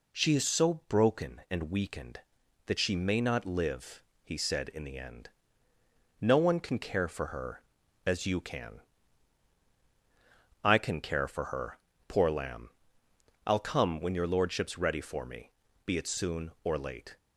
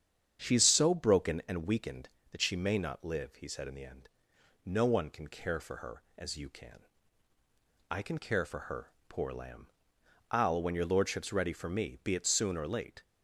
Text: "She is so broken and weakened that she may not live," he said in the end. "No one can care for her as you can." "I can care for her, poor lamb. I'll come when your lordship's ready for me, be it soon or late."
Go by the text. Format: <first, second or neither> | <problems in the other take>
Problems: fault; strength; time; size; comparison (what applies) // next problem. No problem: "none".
first | starts louder than the rest; strong; until 1.4 s; 8 dB // skips "come"; at 10.6 s